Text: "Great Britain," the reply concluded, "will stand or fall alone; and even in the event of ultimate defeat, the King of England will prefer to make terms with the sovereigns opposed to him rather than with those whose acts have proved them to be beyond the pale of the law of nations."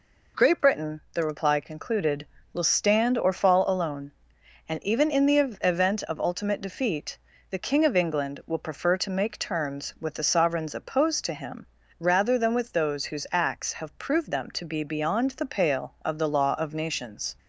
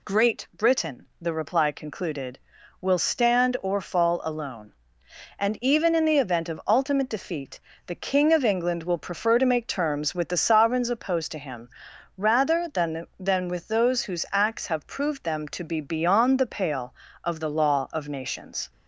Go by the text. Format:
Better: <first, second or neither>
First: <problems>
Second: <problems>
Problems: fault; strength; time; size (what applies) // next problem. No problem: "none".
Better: first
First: pauses between "him" and "rather"; slight; at 11.6 s; 0.34 s long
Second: pauses between "him" and "rather"; noticeable; at 11.6 s; 0.48 s long // says "than" twice; at 13.1 s